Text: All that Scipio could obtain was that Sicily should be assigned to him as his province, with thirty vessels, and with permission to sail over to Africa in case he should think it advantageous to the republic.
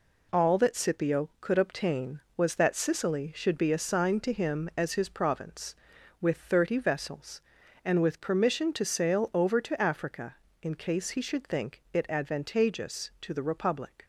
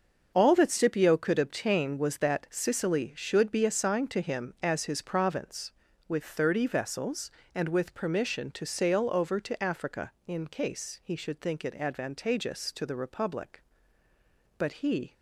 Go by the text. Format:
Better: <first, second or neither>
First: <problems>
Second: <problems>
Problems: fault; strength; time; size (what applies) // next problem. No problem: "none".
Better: first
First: none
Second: starts louder than the rest; until 1.3 s; 7 dB // goes on to say "But he"; from 14.5 s on; 0.54 s long